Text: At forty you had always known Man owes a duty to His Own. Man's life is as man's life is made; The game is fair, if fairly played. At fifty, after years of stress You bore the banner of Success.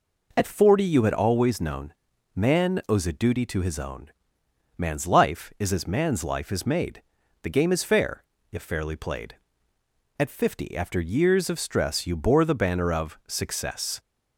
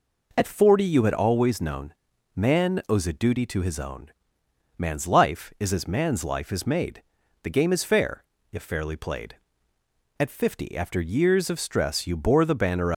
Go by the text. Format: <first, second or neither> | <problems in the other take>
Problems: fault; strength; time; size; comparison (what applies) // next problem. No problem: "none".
first | pauses between "known" and "Man"; at 1.9 s; 0.40 s long; also in the first // stops before "of Success"; at 12.9 s